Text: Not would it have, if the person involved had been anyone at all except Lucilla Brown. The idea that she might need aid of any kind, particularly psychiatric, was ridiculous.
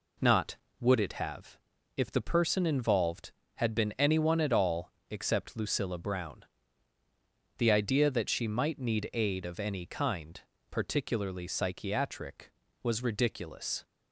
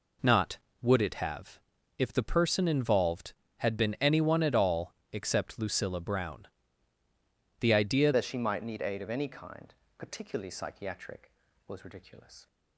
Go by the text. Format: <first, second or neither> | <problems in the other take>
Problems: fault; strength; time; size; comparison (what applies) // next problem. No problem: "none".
first | pauses between "all" and "except"; slight; at 4.9 s; 0.20 s long; slight in the first // changes voice at "that"; from 8.1 s on; 4.3 s long